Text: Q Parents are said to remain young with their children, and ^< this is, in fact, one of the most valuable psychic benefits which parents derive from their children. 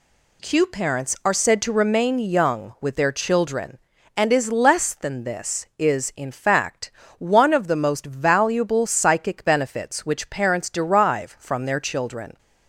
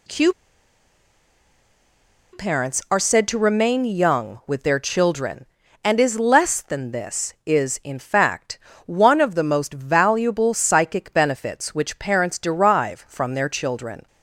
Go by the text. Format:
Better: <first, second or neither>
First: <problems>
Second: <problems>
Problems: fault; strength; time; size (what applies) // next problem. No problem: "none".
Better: first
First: none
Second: pauses between "Q" and "Parents"; strong; at 0.3 s; 2.0 s long